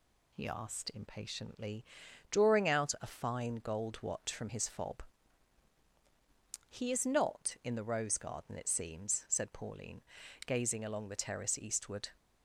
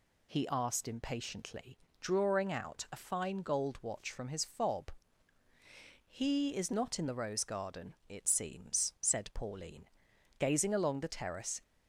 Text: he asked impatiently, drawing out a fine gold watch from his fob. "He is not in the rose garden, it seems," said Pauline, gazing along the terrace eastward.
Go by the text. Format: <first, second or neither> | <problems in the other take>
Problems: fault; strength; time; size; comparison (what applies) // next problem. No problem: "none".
first | stops before "eastward"; at 11.6 s